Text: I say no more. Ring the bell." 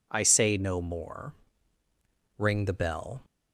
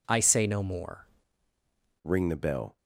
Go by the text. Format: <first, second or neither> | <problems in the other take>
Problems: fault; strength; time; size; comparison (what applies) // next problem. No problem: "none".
first | changes voice at "Ring"; from 2.0 s on; 0.7 s long